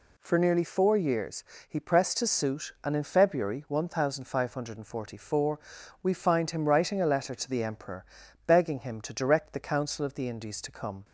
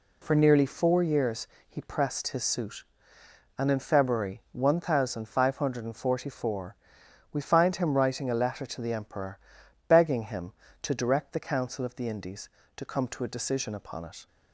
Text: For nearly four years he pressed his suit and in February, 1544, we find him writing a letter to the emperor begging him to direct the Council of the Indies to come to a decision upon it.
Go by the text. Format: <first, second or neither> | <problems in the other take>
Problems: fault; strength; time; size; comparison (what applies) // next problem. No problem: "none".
second | pauses between "years" and "he"; slight; at 1.4 s; 0.26 s long; slight in the second // pauses between "emperor" and "begging"; at 8.0 s; 0.42 s long; noticeable in the second // stops before "to a decision upon it"; at 11.0 s